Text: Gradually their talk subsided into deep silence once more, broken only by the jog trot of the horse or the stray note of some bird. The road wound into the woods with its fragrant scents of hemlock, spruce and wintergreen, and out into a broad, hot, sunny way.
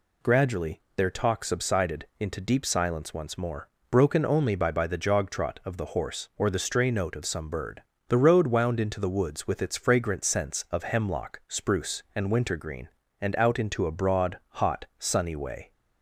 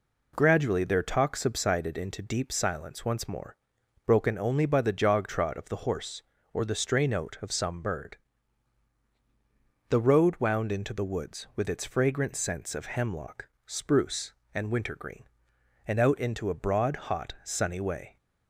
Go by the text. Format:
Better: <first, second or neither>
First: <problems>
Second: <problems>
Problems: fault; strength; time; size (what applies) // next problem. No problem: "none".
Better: second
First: pauses between "Gradually" and "their"; slight; at 0.8 s; 0.16 s long // says "by" twice; at 4.7 s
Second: none